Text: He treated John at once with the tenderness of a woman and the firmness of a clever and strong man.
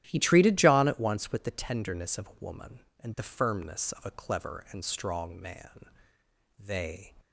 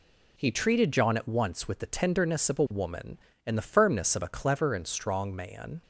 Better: second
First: starts louder than the rest; strong; until 1.0 s; 12 dB // goes on to say "They"; from 6.5 s on; 0.54 s long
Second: none

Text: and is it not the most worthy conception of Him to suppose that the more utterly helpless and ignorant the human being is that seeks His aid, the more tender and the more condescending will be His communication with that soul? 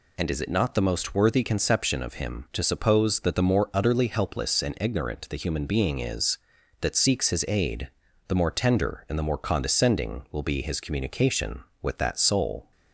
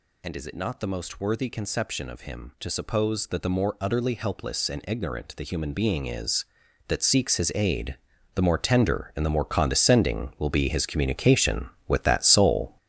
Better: first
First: none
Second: gets louder; strong; throughout; 9 dB

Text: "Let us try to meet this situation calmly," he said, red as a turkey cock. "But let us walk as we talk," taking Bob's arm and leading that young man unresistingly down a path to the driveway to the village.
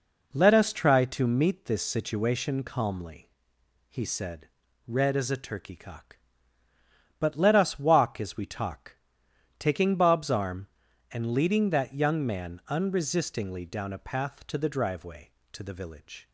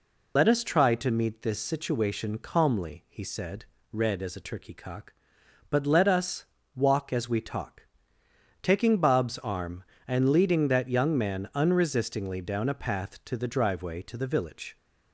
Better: first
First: none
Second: loses the start of "Let"; at 0.3 s; 95 ms // pauses between "us" and "walk"; slight; at 6.4 s; 0.28 s long

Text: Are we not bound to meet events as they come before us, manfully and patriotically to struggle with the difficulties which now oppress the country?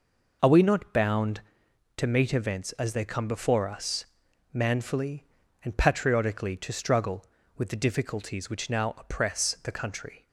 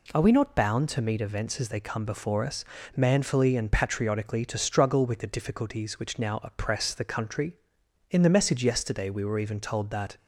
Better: first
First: none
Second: goes on to say "In the message yesterday we were even told that"; strong; from 8.0 s on; 2.0 s long

